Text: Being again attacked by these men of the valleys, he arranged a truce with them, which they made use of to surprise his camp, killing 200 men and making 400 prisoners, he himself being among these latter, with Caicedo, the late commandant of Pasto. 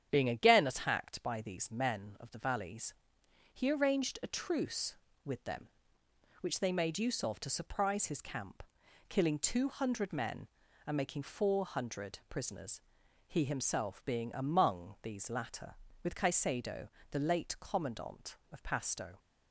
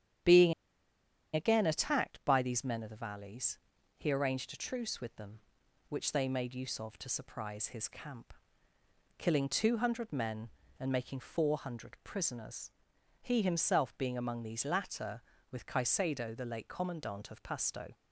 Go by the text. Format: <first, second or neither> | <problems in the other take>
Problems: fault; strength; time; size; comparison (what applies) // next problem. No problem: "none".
first | starts louder than the rest; strong; until 2.0 s; 9.5 dB; strong in the first // pauses between "Being" and "again"; noticeable; at 0.5 s; 0.81 s long